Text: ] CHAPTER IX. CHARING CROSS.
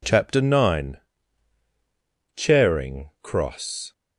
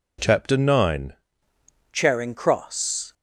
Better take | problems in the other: first | changes voice at "CHARING"; from 1.9 s on; 1.2 s long

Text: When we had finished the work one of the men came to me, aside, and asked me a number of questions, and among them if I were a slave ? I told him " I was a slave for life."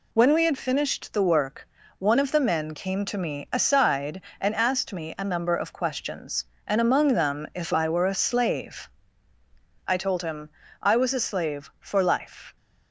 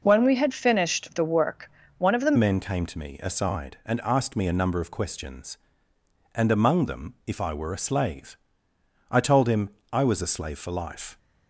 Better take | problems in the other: first | pauses between "work" and "one"; slight; at 1.7 s; 0.26 s long; slight in the first // changes voice at "men"; from 2.3 s on; 8.8 s long

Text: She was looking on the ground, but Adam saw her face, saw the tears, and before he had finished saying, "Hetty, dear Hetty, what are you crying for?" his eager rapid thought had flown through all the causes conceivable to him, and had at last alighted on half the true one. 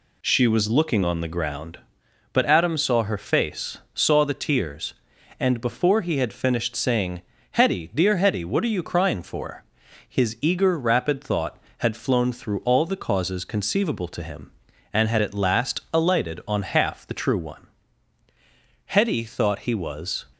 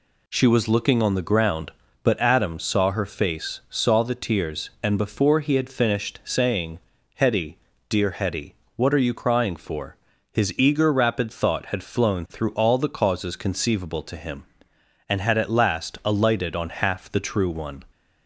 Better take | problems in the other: second | goes on to say "Hetty thought he was"; from 18.8 s on; 1.3 s long

